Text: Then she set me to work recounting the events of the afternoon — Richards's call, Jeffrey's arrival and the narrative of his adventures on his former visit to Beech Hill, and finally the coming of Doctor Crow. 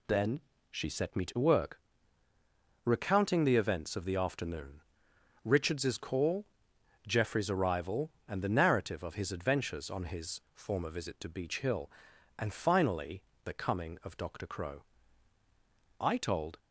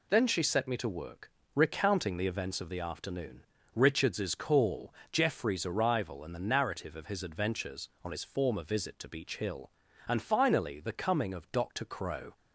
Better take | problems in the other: second | pauses between "Then" and "she"; slight; at 0.4 s; 0.30 s long // pauses between "work" and "recounting"; at 1.7 s; 1.0 s long; slight in the second // pauses between "finally" and "the"; slight; at 13.2 s; 0.22 s long // goes on to say "I told"; from 16.0 s on; 0.58 s long

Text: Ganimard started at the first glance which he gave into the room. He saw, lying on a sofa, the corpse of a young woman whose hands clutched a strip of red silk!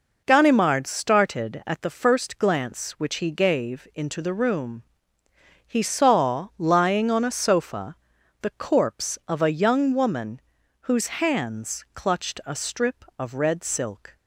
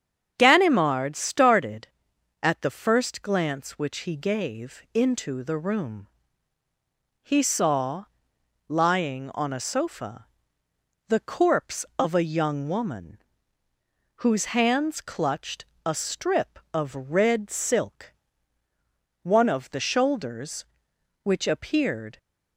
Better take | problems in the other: first | starts louder than the rest; strong; until 1.3 s; 7.5 dB // pauses between "woman" and "whose"; noticeable; at 13.2 s; 0.94 s long; also in the first // pauses between "clutched" and "a"; slight; at 15.6 s; 0.22 s long // goes on to say "One of the shoulders which appeared"; strong; from 19.2 s on; 2.9 s long

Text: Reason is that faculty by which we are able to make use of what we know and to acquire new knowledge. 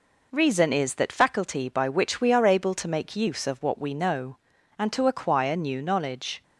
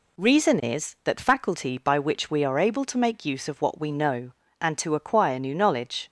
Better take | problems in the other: neither | none

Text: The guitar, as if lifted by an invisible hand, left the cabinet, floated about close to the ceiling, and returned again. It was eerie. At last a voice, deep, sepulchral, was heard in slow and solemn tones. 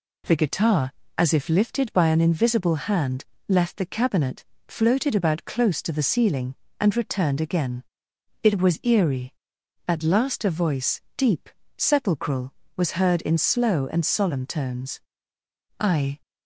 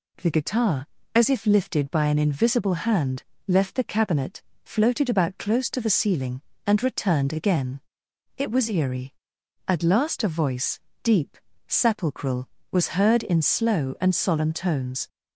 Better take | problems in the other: second | goes on to say "I"; slight; from 15.7 s on; 0.42 s long

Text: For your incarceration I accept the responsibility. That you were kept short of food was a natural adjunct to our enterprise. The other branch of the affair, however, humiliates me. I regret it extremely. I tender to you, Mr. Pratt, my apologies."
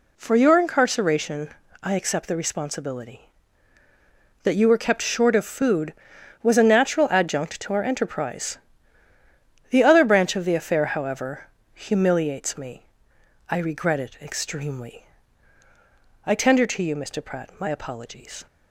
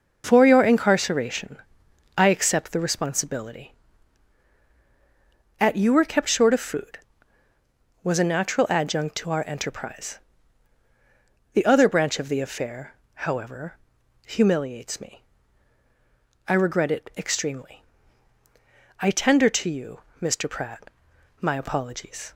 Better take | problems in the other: first | pauses between "incarceration" and "I"; noticeable; at 1.5 s; 0.60 s long; slight in the first // says "At" for "That"; at 5.5 s

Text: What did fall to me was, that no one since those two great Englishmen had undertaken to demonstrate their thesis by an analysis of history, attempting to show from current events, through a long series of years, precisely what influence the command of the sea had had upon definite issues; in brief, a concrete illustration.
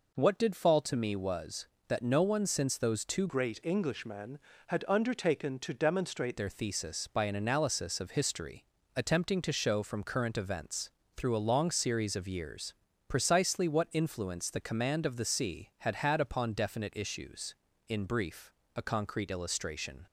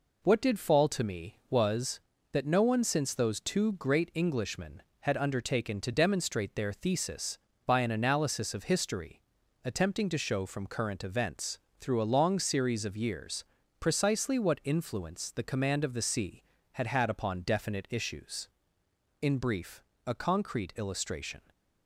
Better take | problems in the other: second | changes voice from "great" to "demonstrate"; from 3.2 to 6.3 s; 3.1 s long

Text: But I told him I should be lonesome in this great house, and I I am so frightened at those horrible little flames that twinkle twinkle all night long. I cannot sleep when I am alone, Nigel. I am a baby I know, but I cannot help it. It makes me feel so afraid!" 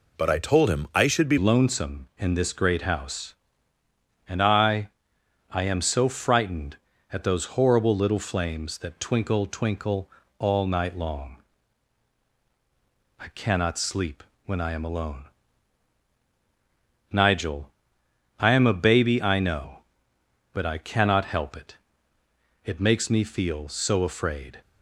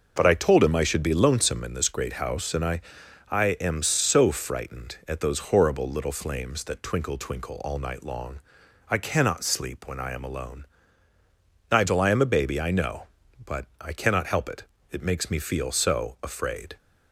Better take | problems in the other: second | changes voice at "lonesome"; from 1.3 s on; 23.2 s long // pauses between "I" and "I"; noticeable; at 4.8 s; 0.60 s long; noticeable in the second // pauses between "twinkle" and "all"; slight; at 10.0 s; 0.28 s long // pauses between "sleep" and "when"; slight; at 14.2 s; 0.22 s long

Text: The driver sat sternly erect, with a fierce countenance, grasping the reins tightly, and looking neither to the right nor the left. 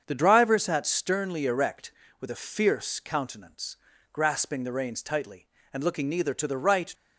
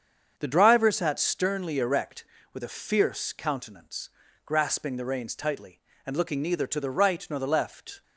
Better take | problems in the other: second | starts louder than the rest; strong; until 1.0 s; 7 dB; strong in the second // stops before "nor the left"; at 6.9 s

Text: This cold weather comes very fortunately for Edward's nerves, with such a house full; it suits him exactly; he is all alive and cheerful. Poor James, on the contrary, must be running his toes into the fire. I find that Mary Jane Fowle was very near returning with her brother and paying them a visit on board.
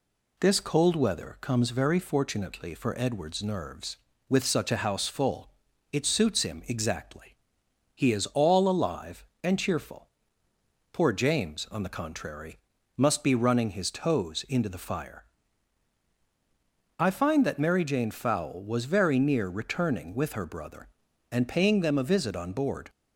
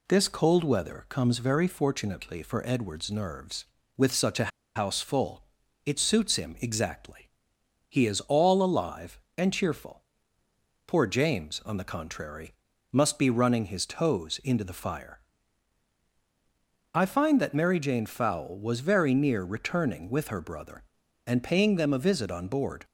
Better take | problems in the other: first | pauses between "a" and "house"; slight; at 4.5 s; 0.26 s long

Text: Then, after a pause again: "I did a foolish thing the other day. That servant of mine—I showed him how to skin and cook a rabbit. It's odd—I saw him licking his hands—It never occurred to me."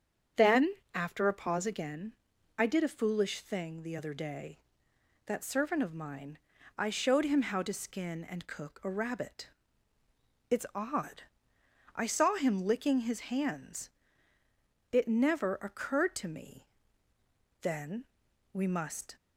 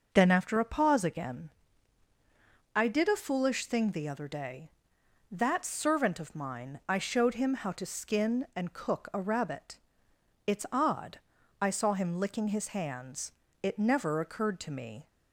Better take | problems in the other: second | starts louder than the rest; strong; until 1.5 s; 7.5 dB // goes on to say "Then We must"; from 17.6 s on; 1.5 s long

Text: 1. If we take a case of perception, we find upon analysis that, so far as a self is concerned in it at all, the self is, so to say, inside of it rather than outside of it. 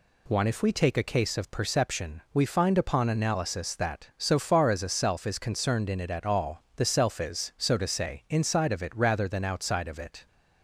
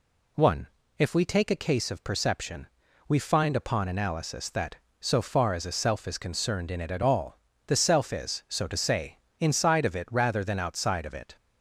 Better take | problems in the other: neither | none

